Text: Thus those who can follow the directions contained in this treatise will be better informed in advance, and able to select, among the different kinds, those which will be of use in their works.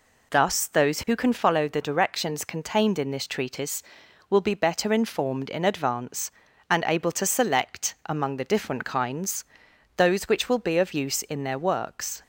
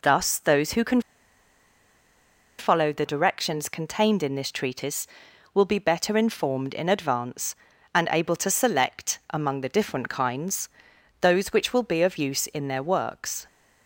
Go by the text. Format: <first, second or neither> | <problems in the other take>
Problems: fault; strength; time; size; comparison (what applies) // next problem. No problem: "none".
first | pauses between "can" and "follow"; strong; at 1.0 s; 1.5 s long